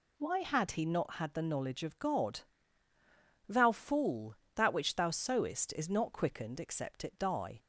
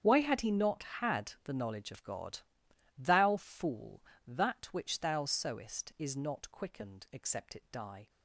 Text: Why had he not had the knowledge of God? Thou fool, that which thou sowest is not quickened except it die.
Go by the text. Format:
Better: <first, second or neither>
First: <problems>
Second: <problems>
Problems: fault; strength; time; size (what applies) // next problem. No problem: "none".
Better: first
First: none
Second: gets quieter; strong; throughout; 16.5 dB